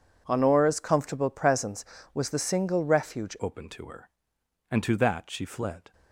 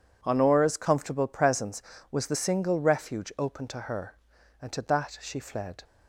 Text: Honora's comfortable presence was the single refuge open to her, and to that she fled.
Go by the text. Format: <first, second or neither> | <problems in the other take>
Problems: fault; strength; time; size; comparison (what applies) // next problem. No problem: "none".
second | changes voice at "open"; from 3.4 s on; 2.5 s long